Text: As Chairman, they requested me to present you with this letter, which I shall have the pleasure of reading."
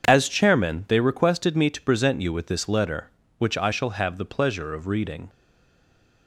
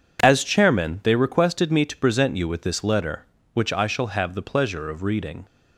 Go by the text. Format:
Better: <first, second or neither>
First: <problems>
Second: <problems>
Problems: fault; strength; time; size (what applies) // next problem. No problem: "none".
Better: second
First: stays silent after the last word; slight; from 5.2 s on; 1.0 s long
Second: none